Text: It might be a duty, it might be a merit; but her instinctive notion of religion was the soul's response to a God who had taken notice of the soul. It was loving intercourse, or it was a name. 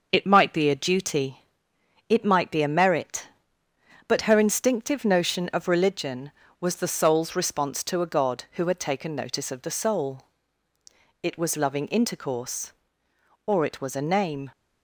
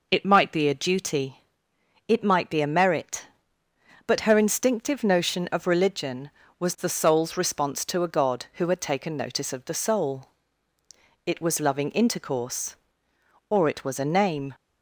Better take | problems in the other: second | gets quieter; slight; throughout; 3 dB

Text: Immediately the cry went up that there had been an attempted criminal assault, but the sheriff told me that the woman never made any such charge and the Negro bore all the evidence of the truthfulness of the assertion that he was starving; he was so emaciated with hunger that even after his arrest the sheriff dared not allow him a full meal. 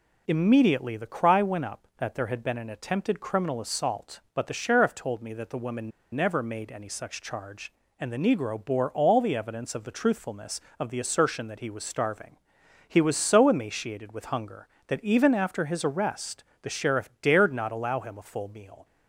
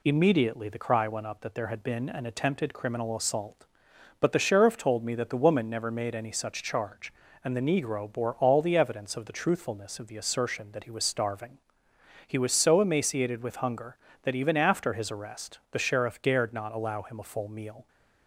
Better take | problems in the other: second | pauses between "woman" and "never"; slight; at 5.9 s; 0.23 s long // pauses between "arrest" and "the"; slight; at 16.4 s; 0.16 s long

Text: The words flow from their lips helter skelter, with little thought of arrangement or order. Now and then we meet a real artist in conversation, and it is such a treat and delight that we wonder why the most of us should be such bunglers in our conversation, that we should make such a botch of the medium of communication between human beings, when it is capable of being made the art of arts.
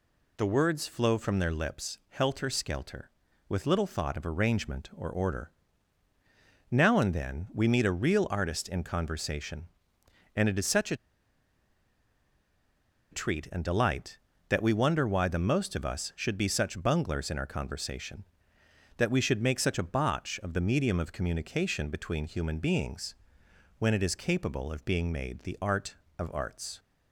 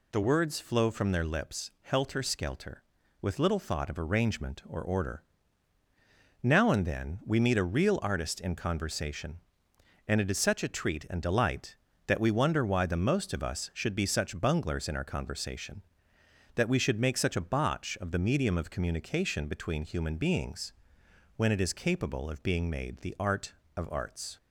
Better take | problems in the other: second | pauses between "a" and "treat"; strong; at 10.9 s; 2.1 s long

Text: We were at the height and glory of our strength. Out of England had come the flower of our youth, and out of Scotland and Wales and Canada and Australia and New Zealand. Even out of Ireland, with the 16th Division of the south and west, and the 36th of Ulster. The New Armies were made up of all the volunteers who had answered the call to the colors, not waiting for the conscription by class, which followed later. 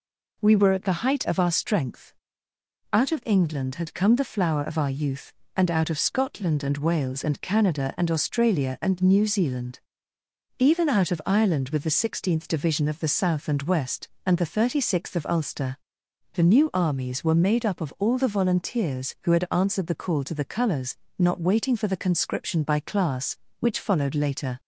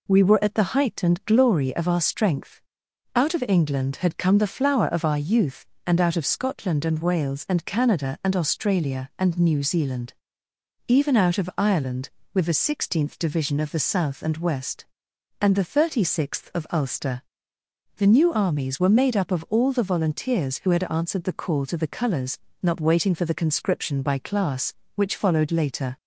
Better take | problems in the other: second | skips "and glory"; at 1.2 s

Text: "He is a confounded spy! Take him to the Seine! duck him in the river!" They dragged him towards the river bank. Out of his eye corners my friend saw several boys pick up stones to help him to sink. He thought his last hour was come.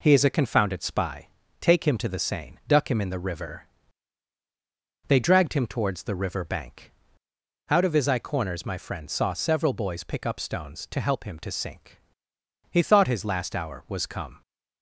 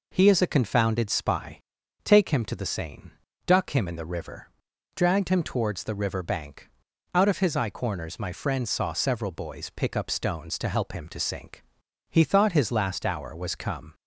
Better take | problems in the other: first | skips "They"; at 4.7 s

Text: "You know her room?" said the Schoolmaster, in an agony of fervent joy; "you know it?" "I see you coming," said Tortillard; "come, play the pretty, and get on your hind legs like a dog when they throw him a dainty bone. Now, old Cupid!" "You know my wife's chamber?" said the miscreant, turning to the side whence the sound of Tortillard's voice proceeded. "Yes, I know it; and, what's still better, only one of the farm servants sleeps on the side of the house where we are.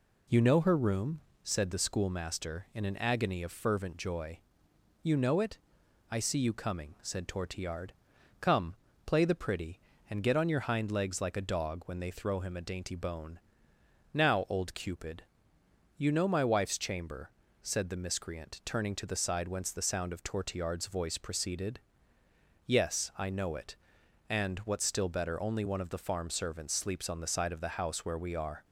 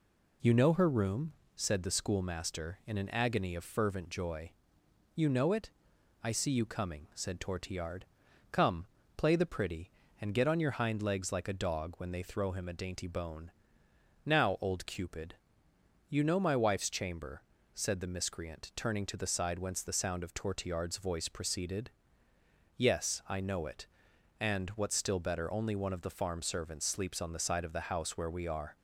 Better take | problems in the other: neither | none

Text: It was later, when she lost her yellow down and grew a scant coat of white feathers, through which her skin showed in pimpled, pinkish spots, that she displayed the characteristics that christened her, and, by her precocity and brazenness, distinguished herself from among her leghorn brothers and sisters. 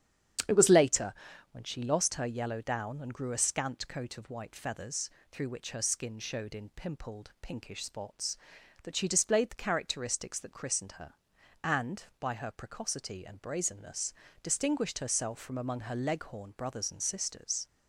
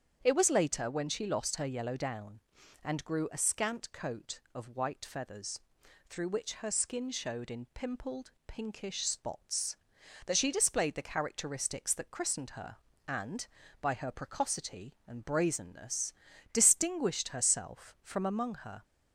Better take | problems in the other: first | starts louder than the rest; strong; until 1.2 s; 8 dB; strong in the first // stops before "leghorn brothers and sisters"; at 18.8 s

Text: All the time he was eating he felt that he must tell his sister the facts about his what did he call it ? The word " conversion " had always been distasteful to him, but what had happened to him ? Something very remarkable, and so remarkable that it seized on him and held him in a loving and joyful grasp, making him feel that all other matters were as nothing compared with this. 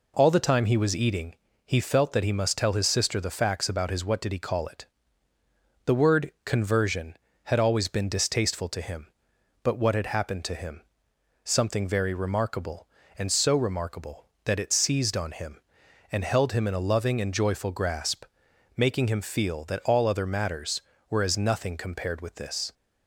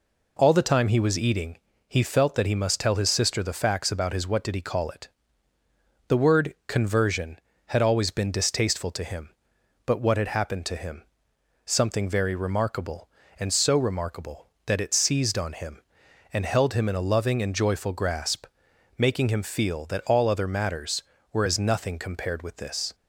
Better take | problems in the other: neither | pauses between "eating" and "he"; slight; the same in both

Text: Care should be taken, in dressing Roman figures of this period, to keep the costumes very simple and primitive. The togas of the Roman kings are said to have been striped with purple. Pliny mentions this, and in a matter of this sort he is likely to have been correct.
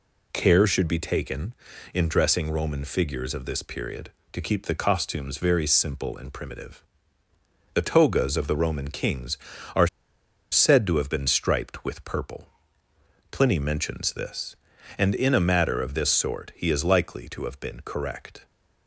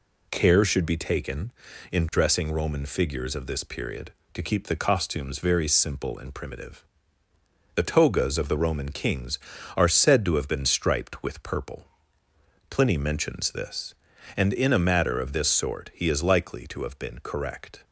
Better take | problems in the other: second | pauses between "are" and "said"; noticeable; at 9.8 s; 0.63 s long

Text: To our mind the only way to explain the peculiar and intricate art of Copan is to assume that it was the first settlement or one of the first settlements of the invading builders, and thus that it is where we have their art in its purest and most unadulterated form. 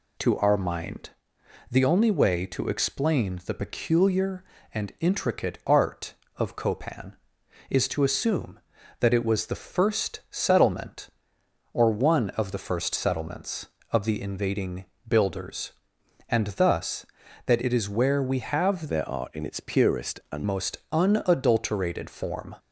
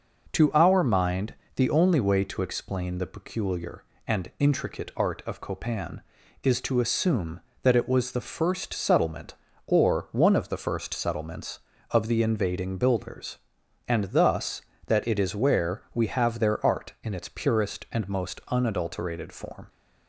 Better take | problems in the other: second | pauses between "mind" and "the"; noticeable; at 1.1 s; 0.58 s long; slight in the second // pauses between "invading" and "builders"; slight; at 14.8 s; 0.20 s long // changes voice from "their" to "and"; from 18.8 to 20.4 s; 1.6 s long

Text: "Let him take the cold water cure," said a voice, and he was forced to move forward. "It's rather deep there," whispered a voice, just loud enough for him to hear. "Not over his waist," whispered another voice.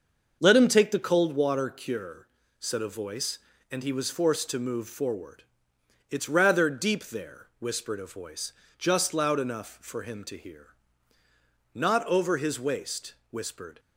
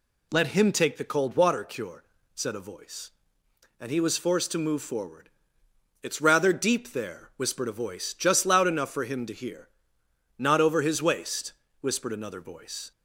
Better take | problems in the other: second | starts louder than the rest; until 1.4 s; 6.5 dB // stops before "another voice"; at 13.7 s

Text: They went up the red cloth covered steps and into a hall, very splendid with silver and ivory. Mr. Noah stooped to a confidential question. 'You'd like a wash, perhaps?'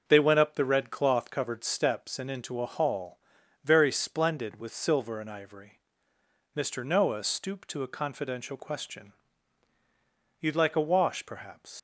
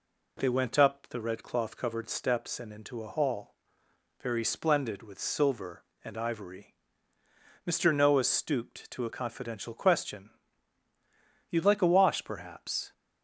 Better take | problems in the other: second | starts louder than the rest; until 1.0 s; 6.5 dB // leaves "perhaps" unfinished; at 11.7 s; 100 ms

